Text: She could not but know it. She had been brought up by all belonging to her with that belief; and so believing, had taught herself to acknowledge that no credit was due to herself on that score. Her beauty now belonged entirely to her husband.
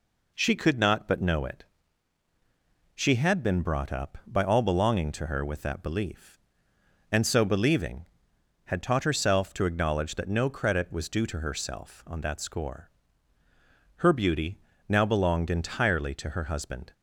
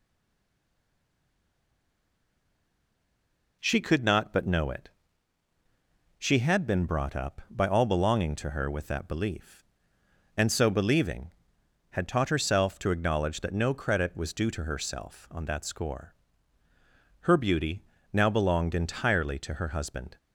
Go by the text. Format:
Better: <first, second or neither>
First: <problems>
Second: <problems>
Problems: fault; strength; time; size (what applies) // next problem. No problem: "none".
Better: first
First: pauses between "beauty" and "now"; slight; at 14.5 s; 0.32 s long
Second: stays silent before the first word; strong; until 3.5 s; 3.5 s long // pauses between "beauty" and "now"; slight; at 17.8 s; 0.32 s long